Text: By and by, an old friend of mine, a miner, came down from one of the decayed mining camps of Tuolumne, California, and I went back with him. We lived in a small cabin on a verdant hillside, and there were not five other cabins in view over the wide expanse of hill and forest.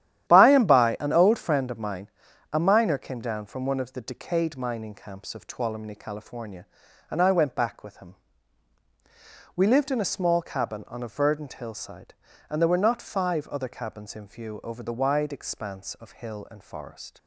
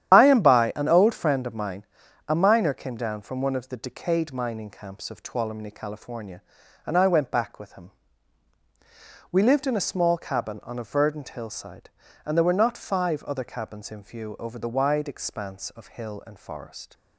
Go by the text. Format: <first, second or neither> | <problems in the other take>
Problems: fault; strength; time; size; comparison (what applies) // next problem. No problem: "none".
first | loses the start of "By"; at 0.1 s; 75 ms // starts louder than the rest; strong; until 1.1 s; 10.5 dB; strong in the first